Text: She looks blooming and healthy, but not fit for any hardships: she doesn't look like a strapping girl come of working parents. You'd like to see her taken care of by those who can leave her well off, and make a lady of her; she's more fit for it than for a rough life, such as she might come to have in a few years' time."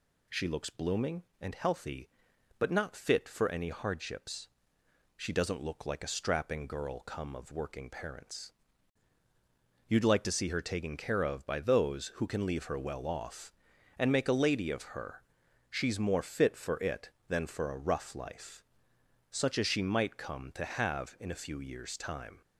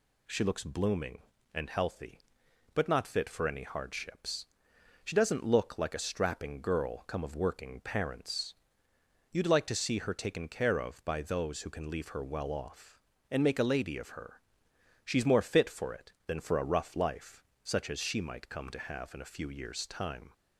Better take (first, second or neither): neither